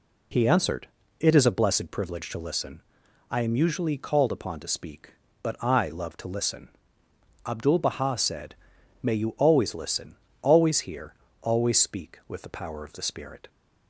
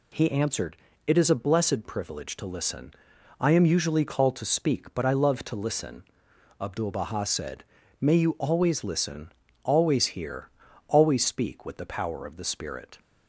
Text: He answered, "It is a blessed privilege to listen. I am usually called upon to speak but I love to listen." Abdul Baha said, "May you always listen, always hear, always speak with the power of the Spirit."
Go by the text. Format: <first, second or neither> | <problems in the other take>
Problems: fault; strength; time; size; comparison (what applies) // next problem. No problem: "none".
first | skips "upon"; at 4.3 s